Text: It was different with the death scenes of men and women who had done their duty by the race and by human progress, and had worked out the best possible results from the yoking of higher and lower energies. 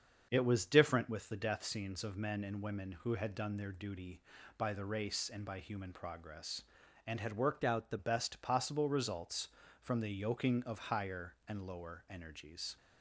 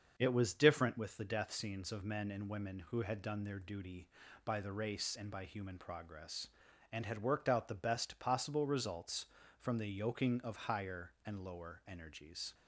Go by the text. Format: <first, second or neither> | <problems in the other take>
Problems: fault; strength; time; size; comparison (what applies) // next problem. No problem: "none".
second | starts louder than the rest; until 1.3 s; 7 dB; also in the second // changes voice from "out" to "the"; from 7.6 to 7.9 s; 0.3 s long